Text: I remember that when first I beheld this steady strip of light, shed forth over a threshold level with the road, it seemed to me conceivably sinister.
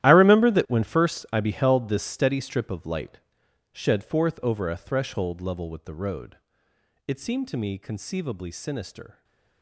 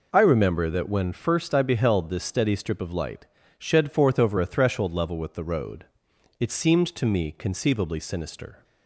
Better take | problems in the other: second | gets quieter; strong; throughout; 16 dB // stays silent after the last word; slight; from 9.1 s on; 0.5 s long

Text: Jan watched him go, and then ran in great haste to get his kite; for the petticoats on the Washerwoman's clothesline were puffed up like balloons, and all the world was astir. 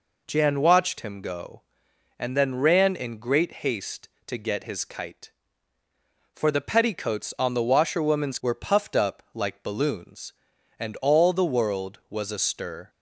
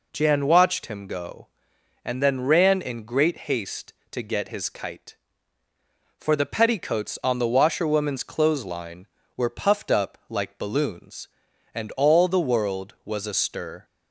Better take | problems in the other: second | skips "clothesline"; at 8.3 s

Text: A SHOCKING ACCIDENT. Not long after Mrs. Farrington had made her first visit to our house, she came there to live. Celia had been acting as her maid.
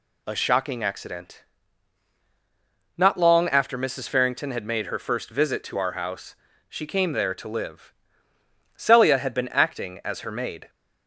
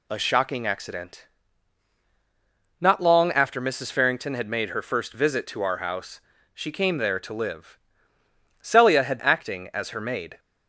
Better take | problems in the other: first | skips "been"; at 9.1 s

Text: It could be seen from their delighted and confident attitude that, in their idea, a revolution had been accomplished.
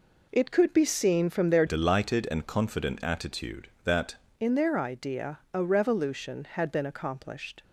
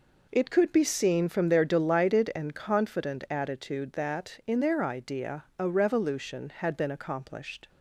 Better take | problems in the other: second | changes voice from "delighted" to "that"; from 1.6 to 4.1 s; 2.5 s long

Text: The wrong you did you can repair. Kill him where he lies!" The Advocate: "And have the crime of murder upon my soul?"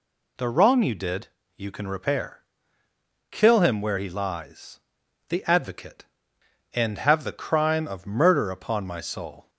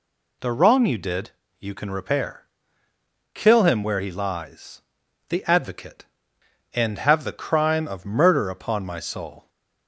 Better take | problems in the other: neither | pauses between "did" and "you"; slight; the same in both

